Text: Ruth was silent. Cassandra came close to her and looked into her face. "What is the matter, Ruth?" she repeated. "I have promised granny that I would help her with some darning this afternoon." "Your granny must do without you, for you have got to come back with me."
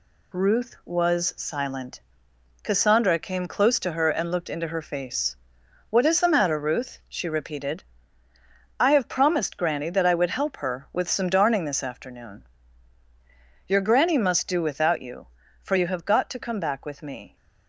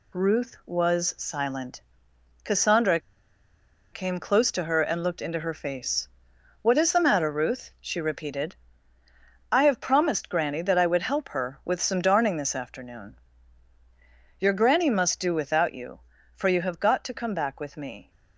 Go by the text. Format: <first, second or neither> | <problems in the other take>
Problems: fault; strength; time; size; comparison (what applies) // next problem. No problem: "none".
first | pauses between "Cassandra" and "came"; noticeable; at 2.9 s; 0.94 s long